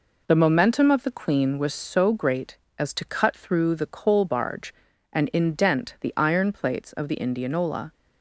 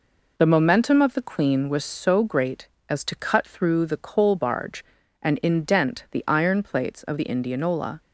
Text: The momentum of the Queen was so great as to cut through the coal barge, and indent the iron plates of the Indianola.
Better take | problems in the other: neither | none

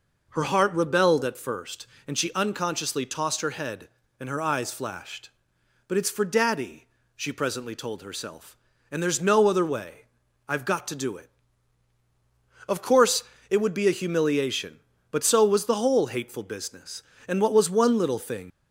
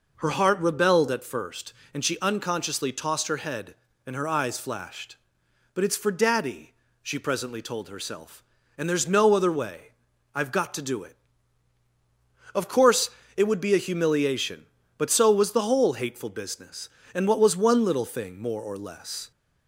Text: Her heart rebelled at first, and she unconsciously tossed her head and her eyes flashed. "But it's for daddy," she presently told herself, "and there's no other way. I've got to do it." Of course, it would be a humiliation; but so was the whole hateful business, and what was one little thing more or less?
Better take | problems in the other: second | stops before "more or less"; at 18.5 s

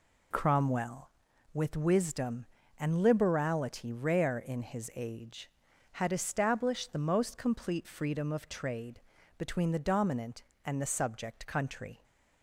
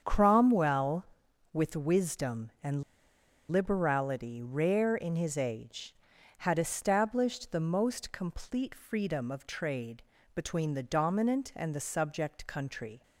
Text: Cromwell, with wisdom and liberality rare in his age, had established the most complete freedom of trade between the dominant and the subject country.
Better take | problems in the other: first | starts louder than the rest; strong; until 1.0 s; 7.5 dB // pauses between "and" and "liberality"; noticeable; at 2.8 s; 0.67 s long // pauses between "trade" and "between"; slight; at 10.0 s; 0.32 s long; slight in the first

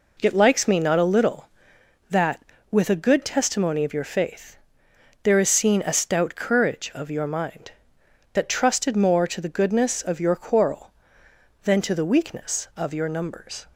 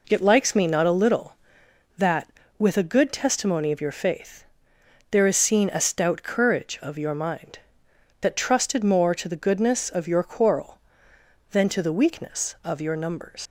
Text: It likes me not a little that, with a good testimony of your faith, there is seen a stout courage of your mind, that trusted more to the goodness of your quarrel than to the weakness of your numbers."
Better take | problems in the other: first | leaves "numbers" unfinished; at 13.4 s; 140 ms

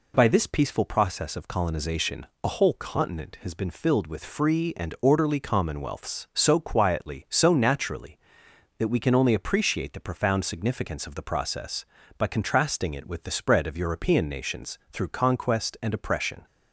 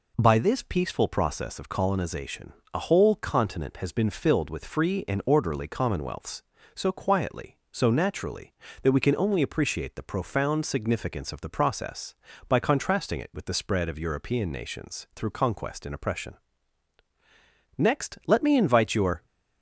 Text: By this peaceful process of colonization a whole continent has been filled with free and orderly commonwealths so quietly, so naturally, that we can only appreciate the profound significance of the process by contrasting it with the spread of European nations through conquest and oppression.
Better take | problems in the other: first | pauses between "colonization" and "a"; slight; at 2.5 s; 0.20 s long; slight in the first // goes on to say "Next let me invite your"; from 17.7 s on; 1.4 s long

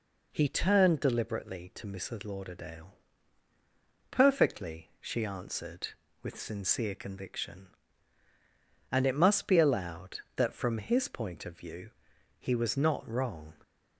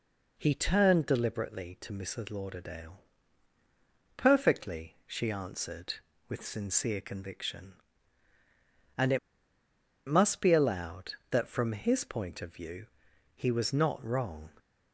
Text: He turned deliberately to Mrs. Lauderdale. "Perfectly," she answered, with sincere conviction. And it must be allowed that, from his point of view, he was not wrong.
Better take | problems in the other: first | pauses between "it" and "must"; noticeable; at 9.1 s; 0.89 s long

